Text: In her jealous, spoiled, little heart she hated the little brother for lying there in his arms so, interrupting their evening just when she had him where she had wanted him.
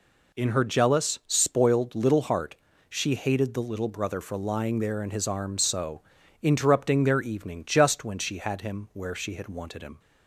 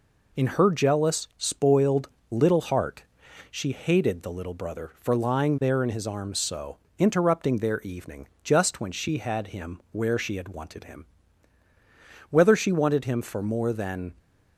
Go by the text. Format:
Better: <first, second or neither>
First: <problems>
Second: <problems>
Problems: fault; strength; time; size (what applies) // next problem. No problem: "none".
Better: first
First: pauses between "heart" and "she"; slight; at 2.5 s; 0.32 s long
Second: pauses between "heart" and "she"; noticeable; at 3.0 s; 0.48 s long // pauses between "evening" and "just"; slight; at 8.2 s; 0.16 s long // goes on to say "Whether she wanted him for more than"; strong; from 12.3 s on; 1.8 s long